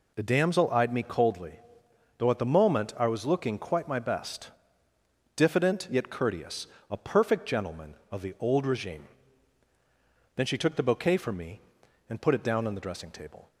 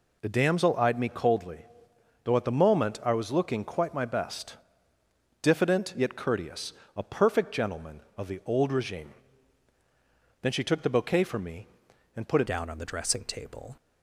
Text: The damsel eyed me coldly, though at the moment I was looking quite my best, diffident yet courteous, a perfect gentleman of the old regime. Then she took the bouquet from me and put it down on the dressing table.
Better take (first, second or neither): first